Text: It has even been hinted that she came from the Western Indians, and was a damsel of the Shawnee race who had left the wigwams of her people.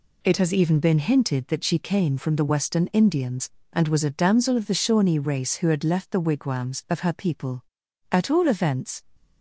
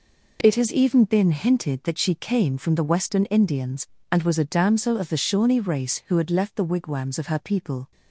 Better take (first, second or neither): second